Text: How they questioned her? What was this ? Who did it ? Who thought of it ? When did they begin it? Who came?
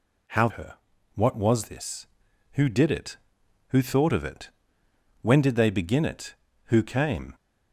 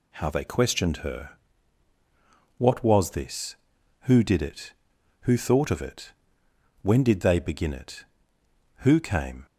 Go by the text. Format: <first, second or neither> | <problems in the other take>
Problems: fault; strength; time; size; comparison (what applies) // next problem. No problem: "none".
second | skips "they questioned"; at 0.4 s